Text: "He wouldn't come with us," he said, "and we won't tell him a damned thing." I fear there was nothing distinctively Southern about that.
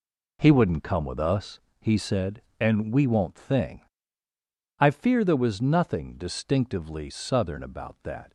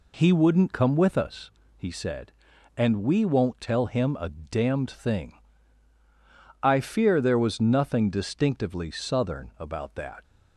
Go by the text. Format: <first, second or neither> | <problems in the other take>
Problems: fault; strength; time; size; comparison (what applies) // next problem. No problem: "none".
second | skips "tell him a damned"; at 3.3 s